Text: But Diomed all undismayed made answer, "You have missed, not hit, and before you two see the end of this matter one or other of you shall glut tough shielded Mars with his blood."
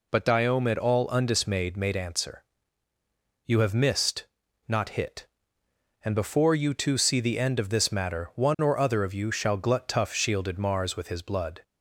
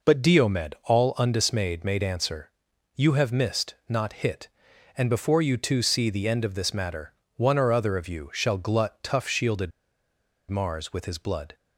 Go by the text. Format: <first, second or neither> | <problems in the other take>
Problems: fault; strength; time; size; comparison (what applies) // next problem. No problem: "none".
first | pauses between "matter" and "one"; slight; at 7.1 s; 0.22 s long // pauses between "shielded" and "Mars"; noticeable; at 9.7 s; 0.78 s long